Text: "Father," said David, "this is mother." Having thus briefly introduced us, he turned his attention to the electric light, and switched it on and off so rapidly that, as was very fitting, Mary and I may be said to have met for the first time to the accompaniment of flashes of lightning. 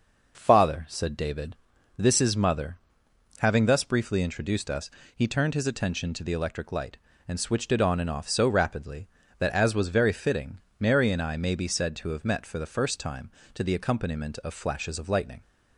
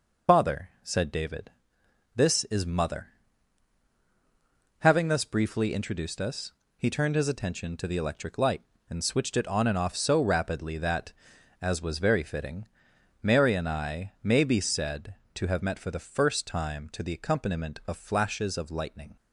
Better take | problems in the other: first | loses the start of "Father"; at 0.2 s; 130 ms

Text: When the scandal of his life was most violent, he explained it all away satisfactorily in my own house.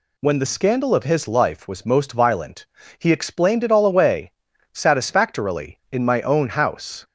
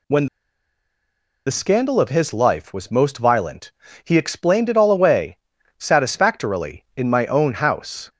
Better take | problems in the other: first | pauses between "When" and "the"; at 0.2 s; 1.2 s long // pauses between "away" and "satisfactorily"; at 5.3 s; 0.42 s long; also in the first

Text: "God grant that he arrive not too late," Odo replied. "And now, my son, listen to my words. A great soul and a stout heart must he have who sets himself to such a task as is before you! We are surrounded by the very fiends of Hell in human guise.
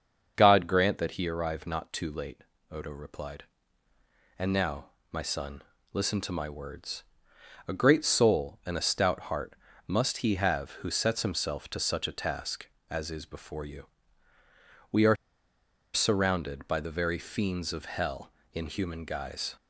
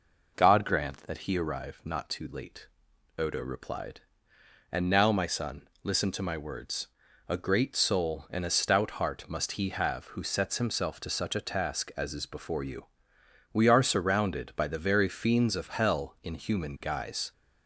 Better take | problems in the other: second | starts louder than the rest; until 1.3 s; 6.5 dB // pauses between "heart" and "must"; slight; at 9.5 s; 0.32 s long // pauses between "are" and "surrounded"; noticeable; at 15.1 s; 0.78 s long

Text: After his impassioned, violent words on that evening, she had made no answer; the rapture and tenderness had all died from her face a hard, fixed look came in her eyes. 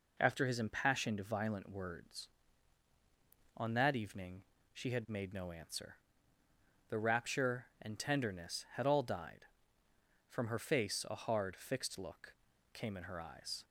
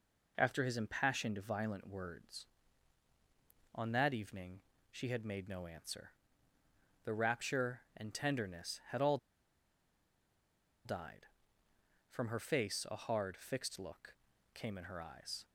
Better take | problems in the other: first | pauses between "all" and "died"; strong; at 9.1 s; 1.6 s long // pauses between "look" and "came"; at 14.1 s; 0.40 s long; also in the first

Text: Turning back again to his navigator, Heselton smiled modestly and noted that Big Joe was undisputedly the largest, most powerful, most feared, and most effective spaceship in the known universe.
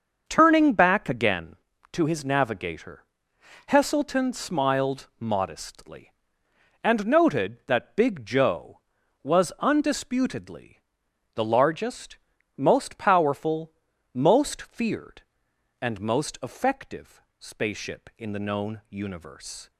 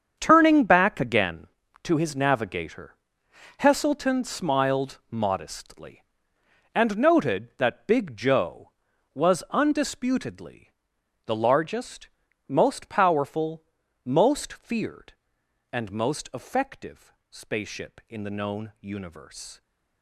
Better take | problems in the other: first | gets quieter; strong; throughout; 13 dB // starts louder than the rest; strong; until 1.2 s; 7.5 dB; also in the first // pauses between "undisputedly" and "the"; noticeable; at 10.7 s; 0.54 s long; noticeable in the first // pauses between "effective" and "spaceship"; slight; at 17.1 s; 0.18 s long; slight in the first

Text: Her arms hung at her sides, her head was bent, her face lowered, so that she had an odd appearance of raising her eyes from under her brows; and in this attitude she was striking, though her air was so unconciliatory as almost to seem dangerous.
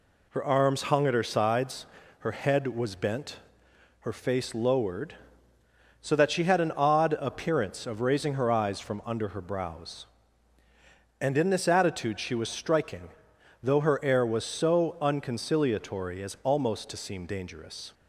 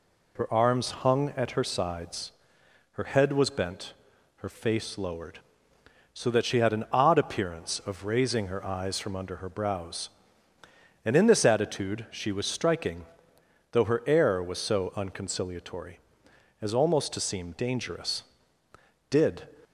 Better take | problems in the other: first | goes on to say "Did"; slight; from 19.0 s on; 0.40 s long

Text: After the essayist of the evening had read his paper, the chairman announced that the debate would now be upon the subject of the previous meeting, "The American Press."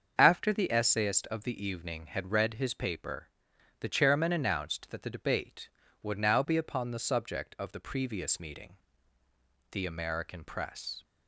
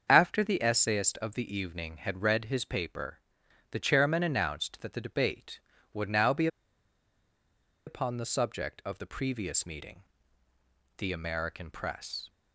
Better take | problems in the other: first | starts louder than the rest; until 1.0 s; 7 dB; also in the first // pauses between "be" and "upon"; strong; at 6.4 s; 1.3 s long

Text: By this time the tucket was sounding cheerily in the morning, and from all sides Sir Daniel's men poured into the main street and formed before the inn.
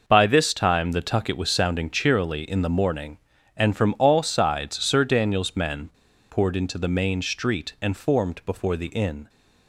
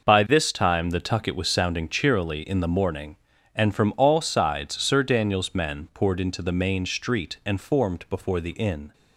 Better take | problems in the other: second | pauses between "men" and "poured"; at 5.9 s; 0.40 s long

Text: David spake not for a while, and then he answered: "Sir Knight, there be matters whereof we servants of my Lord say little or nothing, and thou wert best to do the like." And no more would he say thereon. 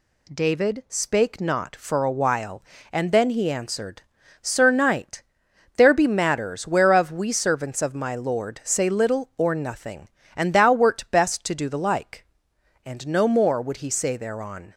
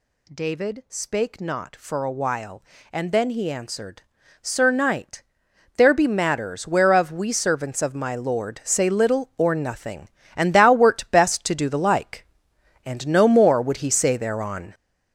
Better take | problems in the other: first | gets louder; strong; throughout; 7.5 dB

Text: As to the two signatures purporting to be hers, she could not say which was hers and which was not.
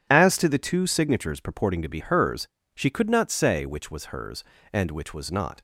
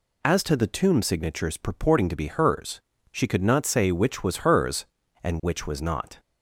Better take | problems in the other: first | says "tomb" for "two"; at 0.6 s

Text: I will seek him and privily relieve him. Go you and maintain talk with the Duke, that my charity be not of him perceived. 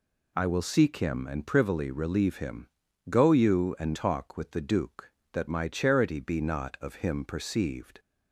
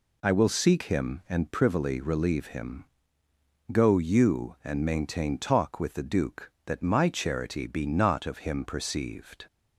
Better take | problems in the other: second | skips "maintain"; at 3.9 s

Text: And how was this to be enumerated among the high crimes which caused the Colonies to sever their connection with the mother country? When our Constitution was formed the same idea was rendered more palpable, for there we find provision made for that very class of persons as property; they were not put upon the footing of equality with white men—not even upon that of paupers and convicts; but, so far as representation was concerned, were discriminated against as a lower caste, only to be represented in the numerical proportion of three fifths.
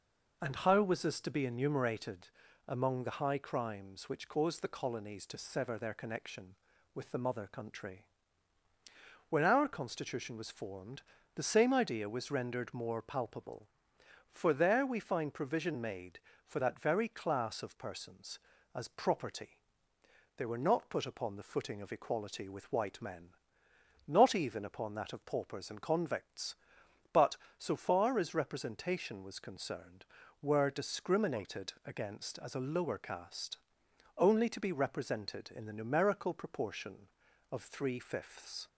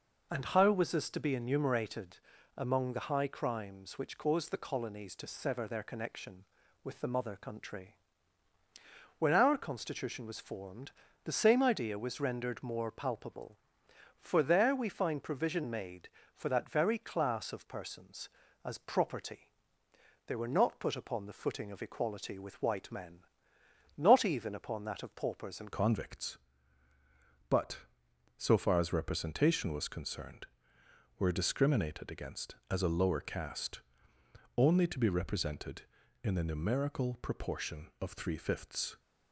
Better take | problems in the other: first | pauses between "enumerated" and "among"; at 2.1 s; 0.40 s long; also in the first // pauses between "formed" and "the"; slight; at 10.9 s; 0.34 s long; slight in the first // changes voice at "convicts"; from 25.7 s on; 13.2 s long

